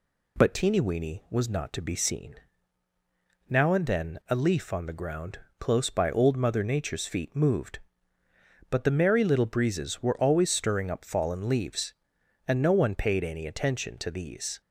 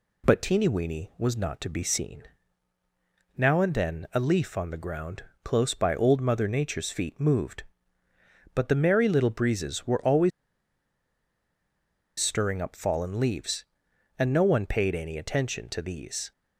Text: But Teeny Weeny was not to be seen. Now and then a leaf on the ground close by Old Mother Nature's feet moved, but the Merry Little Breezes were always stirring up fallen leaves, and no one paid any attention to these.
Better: first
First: pauses between "ground" and "close"; slight; at 5.3 s; 0.20 s long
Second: pauses between "ground" and "close"; slight; at 5.2 s; 0.20 s long // pauses between "always" and "stirring"; strong; at 10.3 s; 1.8 s long

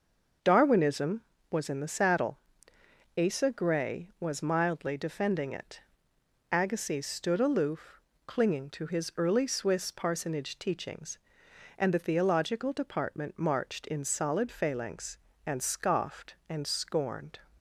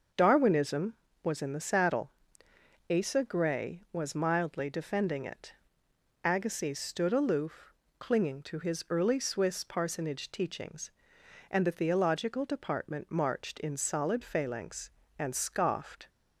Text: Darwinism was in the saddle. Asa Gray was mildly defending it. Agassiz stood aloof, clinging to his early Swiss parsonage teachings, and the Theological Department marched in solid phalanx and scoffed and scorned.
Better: first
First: starts louder than the rest; until 1.7 s; 6.5 dB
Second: starts louder than the rest; until 1.4 s; 6.5 dB // stops before "and scorned"; at 16.0 s

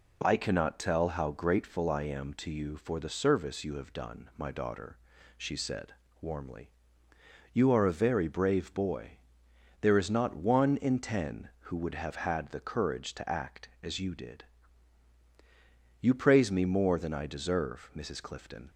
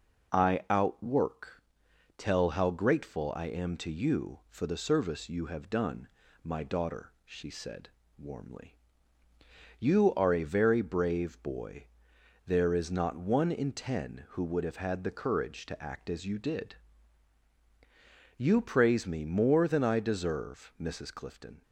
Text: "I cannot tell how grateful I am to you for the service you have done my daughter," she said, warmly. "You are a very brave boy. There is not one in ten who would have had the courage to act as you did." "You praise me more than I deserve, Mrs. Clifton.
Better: first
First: none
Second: says "outwork" for "cannot"; at 0.7 s // pauses between "done" and "my"; at 6.0 s; 0.38 s long

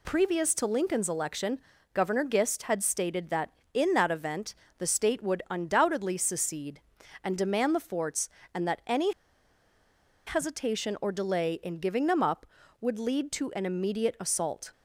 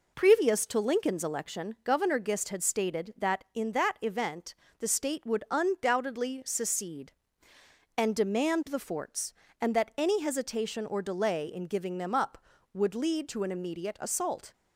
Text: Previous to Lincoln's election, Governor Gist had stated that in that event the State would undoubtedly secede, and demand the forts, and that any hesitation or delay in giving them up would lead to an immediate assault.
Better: second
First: pauses between "event" and "the"; slight; at 4.5 s; 0.24 s long // pauses between "any" and "hesitation"; at 9.1 s; 1.1 s long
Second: pauses between "event" and "the"; slight; at 4.5 s; 0.24 s long

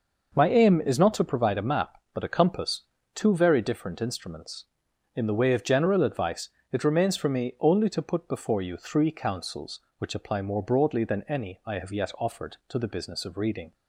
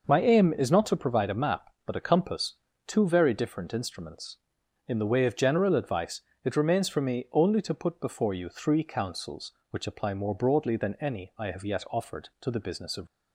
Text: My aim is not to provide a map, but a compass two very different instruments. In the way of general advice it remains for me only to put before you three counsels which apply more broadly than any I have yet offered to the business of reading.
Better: first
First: pauses between "compass" and "two"; slight; at 2.8 s; 0.32 s long // pauses between "advice" and "it"; slight; at 6.4 s; 0.22 s long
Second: pauses between "compass" and "two"; slight; at 2.5 s; 0.32 s long // pauses between "advice" and "it"; slight; at 6.2 s; 0.22 s long // stops before "reading"; at 13.0 s

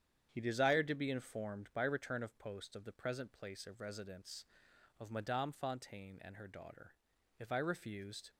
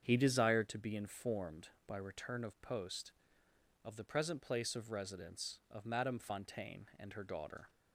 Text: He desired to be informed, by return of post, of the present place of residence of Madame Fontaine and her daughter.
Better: second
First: starts louder than the rest; strong; until 1.3 s; 9 dB // goes on to say "If I refused"; noticeable; from 7.3 s on; 0.92 s long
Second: starts louder than the rest; strong; until 1.0 s; 7.5 dB

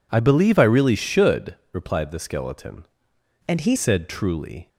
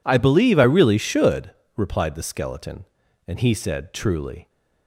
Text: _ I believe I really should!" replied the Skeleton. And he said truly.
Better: second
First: changes voice from "And" to "he"; from 3.4 to 3.7 s; 0.3 s long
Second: none

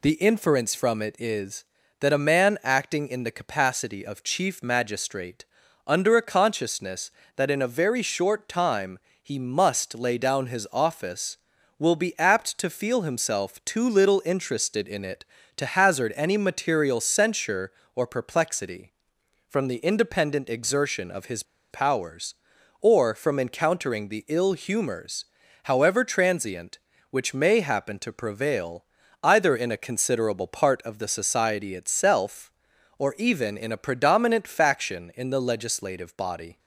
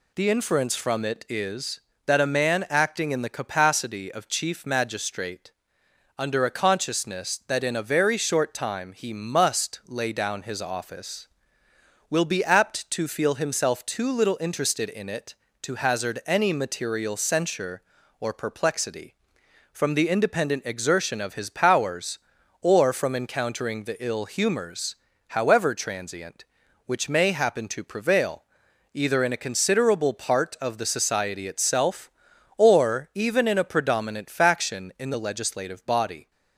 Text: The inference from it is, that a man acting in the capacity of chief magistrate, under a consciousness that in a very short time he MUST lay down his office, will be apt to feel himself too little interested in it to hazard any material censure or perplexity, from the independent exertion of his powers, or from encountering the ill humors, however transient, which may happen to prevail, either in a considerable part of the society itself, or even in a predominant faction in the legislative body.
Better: second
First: pauses between "time" and "he"; slight; at 8.9 s; 0.24 s long // pauses between "his" and "powers"; slight; at 21.4 s; 0.28 s long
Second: none

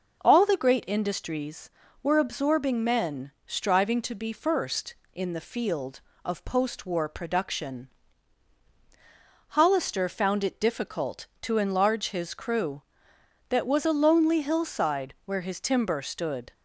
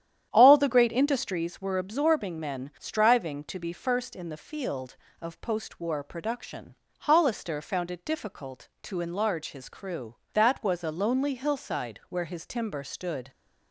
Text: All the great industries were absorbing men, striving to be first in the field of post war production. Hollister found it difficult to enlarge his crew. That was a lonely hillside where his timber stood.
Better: first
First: none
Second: starts louder than the rest; strong; until 1.5 s; 10.5 dB

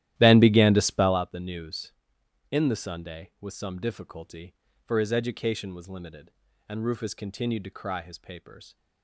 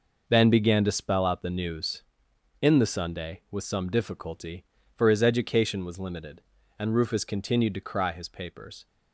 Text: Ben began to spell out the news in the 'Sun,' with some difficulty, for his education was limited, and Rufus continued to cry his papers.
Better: second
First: starts louder than the rest; strong; until 1.3 s; 13.5 dB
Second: none

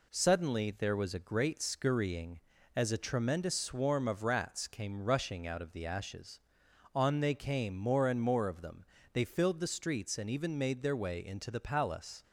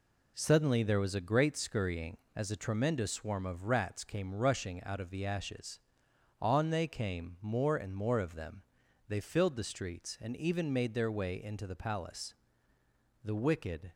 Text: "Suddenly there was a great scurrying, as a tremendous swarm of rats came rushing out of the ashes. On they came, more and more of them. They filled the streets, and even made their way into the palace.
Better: first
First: none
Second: goes on to say "The wicked"; noticeable; from 13.2 s on; 0.70 s long

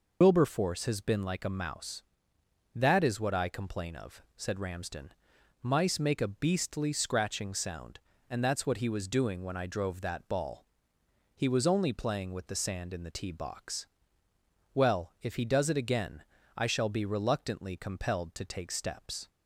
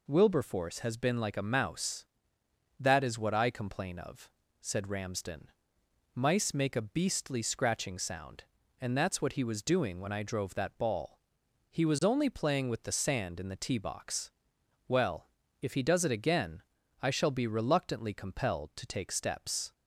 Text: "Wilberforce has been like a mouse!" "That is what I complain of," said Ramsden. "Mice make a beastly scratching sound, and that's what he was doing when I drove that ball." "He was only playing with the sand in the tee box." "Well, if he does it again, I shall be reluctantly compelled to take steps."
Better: second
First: loses the start of "Wilberforce"; at 0.2 s; 80 ms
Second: none

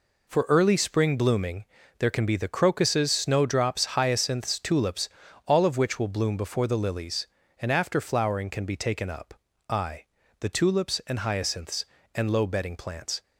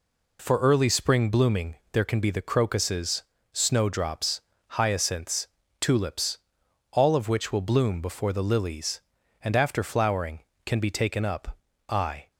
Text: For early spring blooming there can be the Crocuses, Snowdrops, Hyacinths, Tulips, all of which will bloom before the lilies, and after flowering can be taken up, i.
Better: second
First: pauses between "blooming" and "there"; slight; at 1.6 s; 0.36 s long // goes on to say "the Tulips and Hyacinths and low bedding plants"; strong; from 10.4 s on; 2.8 s long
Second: pauses between "blooming" and "there"; slight; at 1.7 s; 0.16 s long

